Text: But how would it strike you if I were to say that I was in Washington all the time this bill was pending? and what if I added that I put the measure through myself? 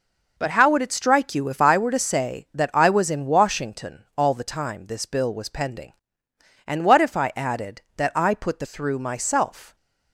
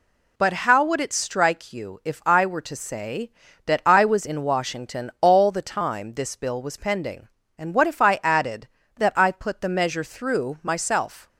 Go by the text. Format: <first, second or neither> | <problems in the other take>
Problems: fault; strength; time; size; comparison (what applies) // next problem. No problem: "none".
second | skips "measure"; at 8.6 s